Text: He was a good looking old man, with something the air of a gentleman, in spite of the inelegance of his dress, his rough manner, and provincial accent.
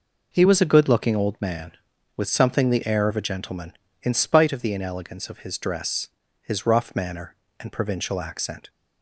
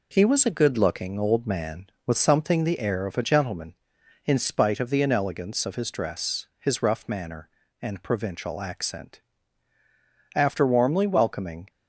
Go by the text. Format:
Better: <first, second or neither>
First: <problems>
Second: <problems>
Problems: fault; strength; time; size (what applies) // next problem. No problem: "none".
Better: first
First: none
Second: goes on to say "After warmly welcoming"; from 10.3 s on; 1.3 s long